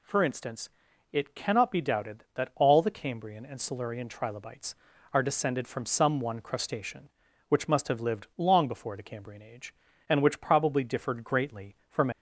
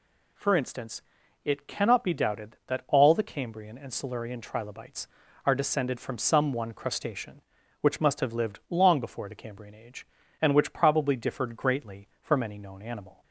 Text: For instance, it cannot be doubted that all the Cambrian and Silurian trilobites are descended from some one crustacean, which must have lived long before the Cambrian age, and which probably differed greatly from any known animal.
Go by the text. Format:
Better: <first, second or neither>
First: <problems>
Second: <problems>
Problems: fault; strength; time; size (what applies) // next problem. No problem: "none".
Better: second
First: stops before "any known animal"; at 12.1 s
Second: none